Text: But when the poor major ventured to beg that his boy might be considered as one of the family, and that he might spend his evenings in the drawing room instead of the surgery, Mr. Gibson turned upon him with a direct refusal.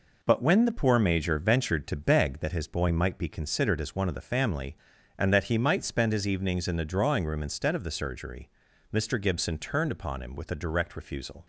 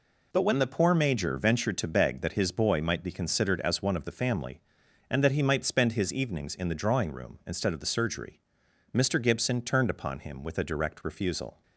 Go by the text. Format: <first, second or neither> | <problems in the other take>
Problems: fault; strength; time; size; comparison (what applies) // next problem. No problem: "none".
neither | none